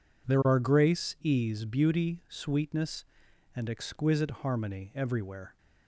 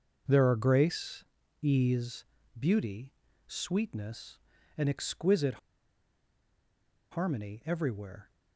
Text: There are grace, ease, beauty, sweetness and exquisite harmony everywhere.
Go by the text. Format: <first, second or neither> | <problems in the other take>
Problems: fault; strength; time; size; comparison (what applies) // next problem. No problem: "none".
first | pauses between "exquisite" and "harmony"; strong; at 5.5 s; 1.5 s long